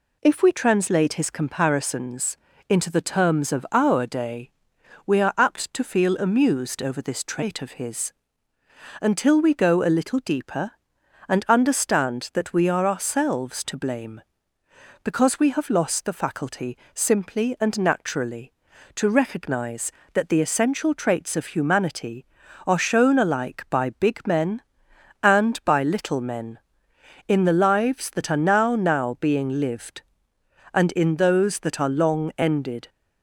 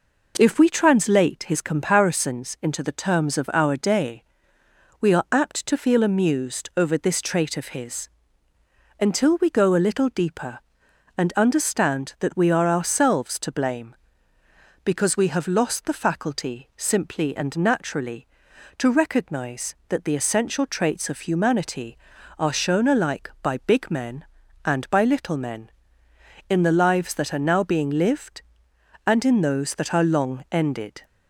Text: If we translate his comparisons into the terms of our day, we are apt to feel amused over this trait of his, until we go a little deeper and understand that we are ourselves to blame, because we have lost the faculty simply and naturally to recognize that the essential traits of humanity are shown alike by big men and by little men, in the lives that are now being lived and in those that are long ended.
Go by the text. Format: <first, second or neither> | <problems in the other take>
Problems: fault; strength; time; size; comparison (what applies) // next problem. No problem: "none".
second | pauses between "comparisons" and "into"; slight; at 2.3 s; 0.32 s long // pauses between "faculty" and "simply"; slight; at 16.7 s; 0.18 s long // says "now" twice; at 28.7 s